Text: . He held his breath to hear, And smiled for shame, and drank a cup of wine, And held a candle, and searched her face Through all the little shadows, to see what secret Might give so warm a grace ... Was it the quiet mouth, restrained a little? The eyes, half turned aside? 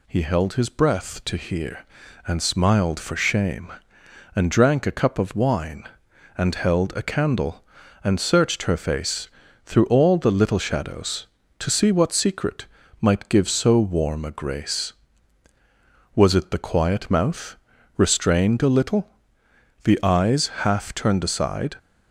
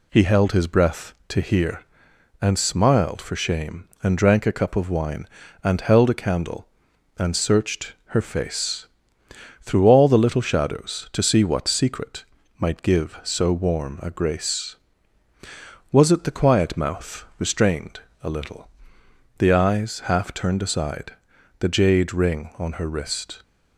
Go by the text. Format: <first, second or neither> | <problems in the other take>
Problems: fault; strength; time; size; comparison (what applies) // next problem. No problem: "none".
first | pauses between "face" and "Through"; noticeable; at 8.8 s; 0.76 s long; slight in the first // pauses between "secret" and "Might"; slight; at 12.2 s; 0.34 s long; slight in the first // pauses between "restrained" and "a"; slight; at 17.9 s; 0.24 s long // goes on to say "The jade ring on her wrist"; strong; from 21.5 s on; 1.8 s long